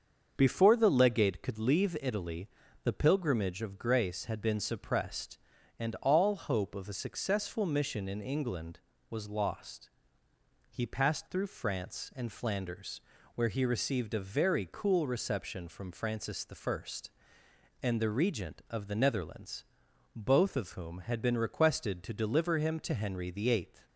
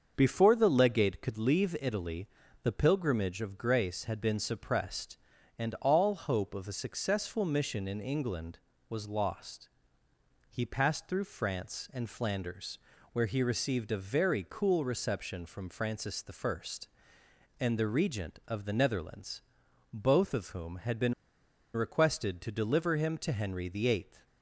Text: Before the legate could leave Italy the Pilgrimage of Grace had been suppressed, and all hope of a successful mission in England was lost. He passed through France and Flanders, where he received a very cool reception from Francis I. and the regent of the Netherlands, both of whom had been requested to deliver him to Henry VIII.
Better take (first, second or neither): first